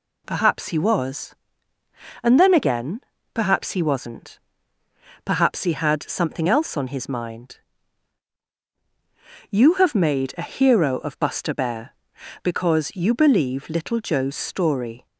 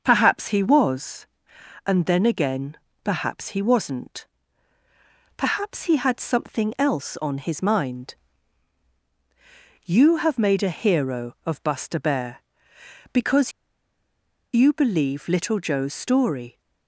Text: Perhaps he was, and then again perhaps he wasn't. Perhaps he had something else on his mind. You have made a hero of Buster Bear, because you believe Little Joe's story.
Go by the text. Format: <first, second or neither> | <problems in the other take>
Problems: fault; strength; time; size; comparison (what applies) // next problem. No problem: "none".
first | starts louder than the rest; until 1.0 s; 6.5 dB // pauses between "again" and "perhaps"; slight; at 2.7 s; 0.28 s long; slight in the first // pauses between "because" and "you"; at 13.5 s; 1.0 s long